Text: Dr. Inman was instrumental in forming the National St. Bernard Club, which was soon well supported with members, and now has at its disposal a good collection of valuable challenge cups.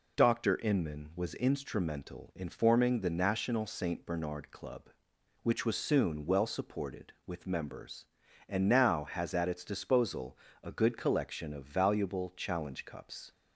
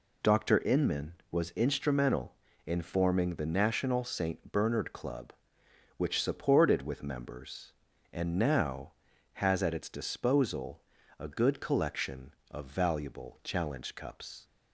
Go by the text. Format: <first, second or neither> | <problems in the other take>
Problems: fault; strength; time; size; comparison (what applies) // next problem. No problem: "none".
first | skips "was soon well"; at 6.2 s // pauses between "disposal" and "a"; slight; at 10.8 s; 0.36 s long; slight in the first